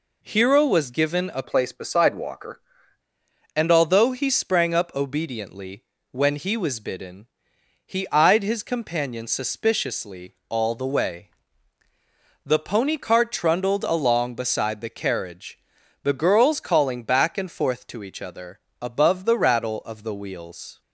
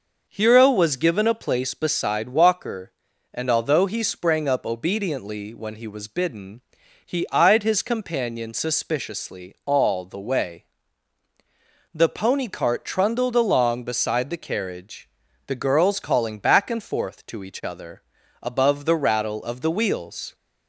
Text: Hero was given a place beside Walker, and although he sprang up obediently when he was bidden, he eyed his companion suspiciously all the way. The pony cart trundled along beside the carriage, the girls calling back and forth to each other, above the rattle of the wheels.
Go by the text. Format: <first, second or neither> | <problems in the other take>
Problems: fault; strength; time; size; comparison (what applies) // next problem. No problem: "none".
second | changes voice from "place" to "Walker"; from 1.4 to 2.5 s; 1.1 s long // pauses between "obediently" and "when"; slight; at 5.8 s; 0.28 s long